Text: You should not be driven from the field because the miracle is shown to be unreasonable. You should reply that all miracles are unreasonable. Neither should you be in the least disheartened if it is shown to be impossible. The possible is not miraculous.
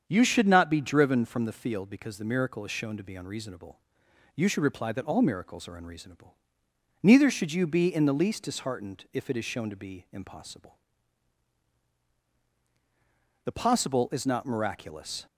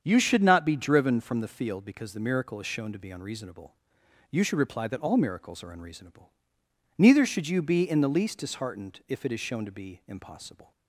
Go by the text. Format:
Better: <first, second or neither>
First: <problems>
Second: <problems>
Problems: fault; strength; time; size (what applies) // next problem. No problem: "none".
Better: first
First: starts louder than the rest; strong; until 1.0 s; 7.5 dB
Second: starts louder than the rest; strong; until 1.0 s; 7.5 dB // stops before "The possible is not miraculous"; at 10.7 s